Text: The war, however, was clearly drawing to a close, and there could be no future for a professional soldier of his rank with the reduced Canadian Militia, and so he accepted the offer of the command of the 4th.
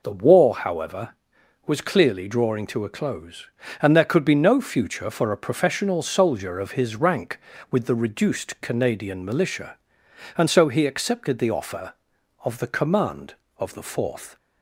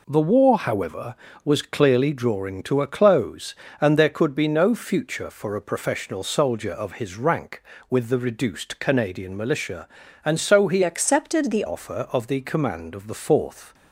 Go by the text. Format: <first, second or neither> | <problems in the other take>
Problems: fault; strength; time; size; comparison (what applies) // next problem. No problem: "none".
first | changes voice from "accepted" to "the"; from 10.8 to 11.6 s; 0.8 s long